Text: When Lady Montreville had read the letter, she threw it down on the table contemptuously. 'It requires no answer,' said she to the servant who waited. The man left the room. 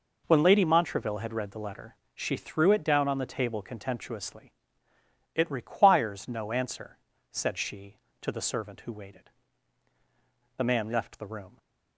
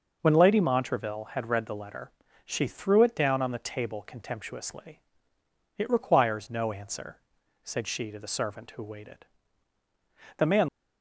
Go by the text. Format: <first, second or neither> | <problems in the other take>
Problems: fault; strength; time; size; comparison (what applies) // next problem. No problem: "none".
first | stops before "left the room"; at 10.6 s